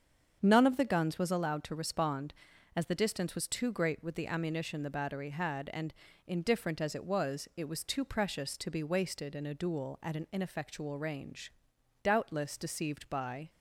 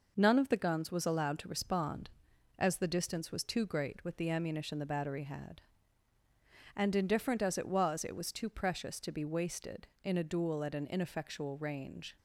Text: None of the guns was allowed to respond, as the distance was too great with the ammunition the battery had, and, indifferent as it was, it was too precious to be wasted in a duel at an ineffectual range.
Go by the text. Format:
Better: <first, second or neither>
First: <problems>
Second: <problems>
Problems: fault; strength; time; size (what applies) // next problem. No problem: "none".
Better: second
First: starts louder than the rest; strong; until 1.4 s; 7 dB // goes on to say "Doubtless deceived by"; from 12.0 s on; 1.4 s long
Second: none